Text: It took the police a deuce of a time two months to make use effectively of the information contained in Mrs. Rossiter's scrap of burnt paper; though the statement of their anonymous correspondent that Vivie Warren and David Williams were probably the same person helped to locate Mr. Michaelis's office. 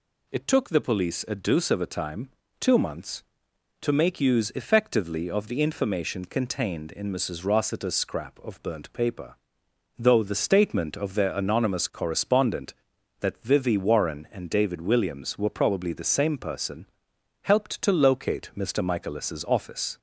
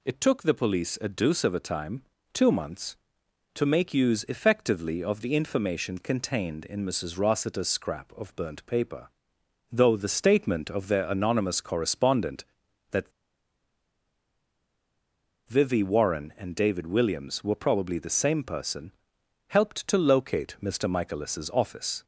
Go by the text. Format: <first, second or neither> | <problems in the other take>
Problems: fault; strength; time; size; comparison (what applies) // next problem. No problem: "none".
first | pauses between "time" and "two"; slight; at 2.0 s; 0.30 s long; slight in the first // pauses between "that" and "Vivie"; strong; at 13.1 s; 2.3 s long // pauses between "person" and "helped"; noticeable; at 18.9 s; 0.56 s long; noticeable in the first